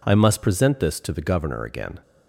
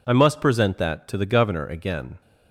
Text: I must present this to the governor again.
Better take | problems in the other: first | says "that" for "this"; at 0.7 s

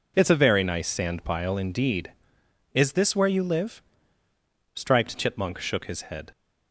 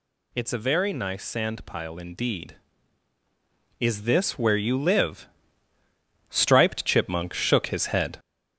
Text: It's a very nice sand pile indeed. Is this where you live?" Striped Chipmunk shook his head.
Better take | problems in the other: first | gets louder; noticeable; throughout; 5 dB

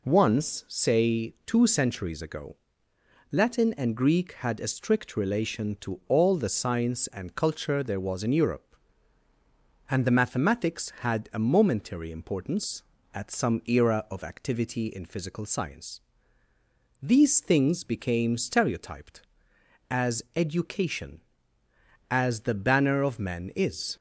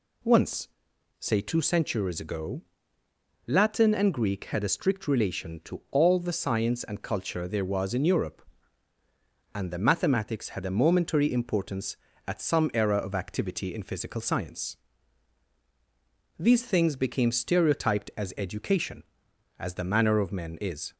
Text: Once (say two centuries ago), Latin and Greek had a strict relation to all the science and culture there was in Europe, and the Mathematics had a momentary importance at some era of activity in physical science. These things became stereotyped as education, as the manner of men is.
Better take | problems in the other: second | says "banner" for "manner"; at 22.5 s

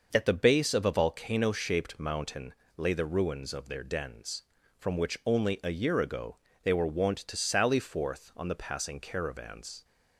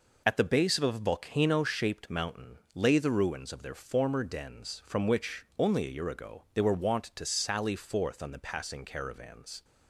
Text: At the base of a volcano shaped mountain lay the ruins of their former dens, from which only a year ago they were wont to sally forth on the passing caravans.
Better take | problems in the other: second | starts louder than the rest; noticeable; until 1.1 s; 6 dB // pauses between "mountain" and "lay"; slight; at 2.5 s; 0.22 s long; slight in the second // skips "former"; at 3.8 s // pauses between "ago" and "they"; slight; at 6.3 s; 0.26 s long

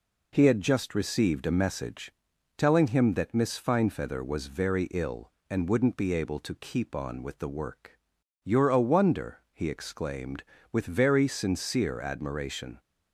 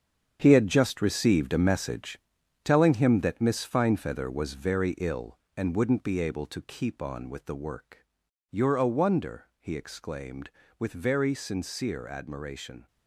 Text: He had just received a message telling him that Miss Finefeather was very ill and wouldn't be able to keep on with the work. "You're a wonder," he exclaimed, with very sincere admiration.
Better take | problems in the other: first | gets quieter; strong; throughout; 10.5 dB // pauses between "message" and "telling"; noticeable; at 2.1 s; 0.48 s long; noticeable in the first

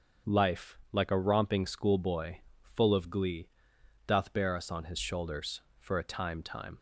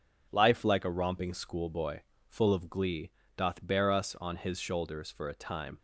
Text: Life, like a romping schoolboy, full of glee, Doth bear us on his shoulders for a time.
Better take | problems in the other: second | starts louder than the rest; until 1.3 s; 6.5 dB // says "time" twice; at 6.4 s

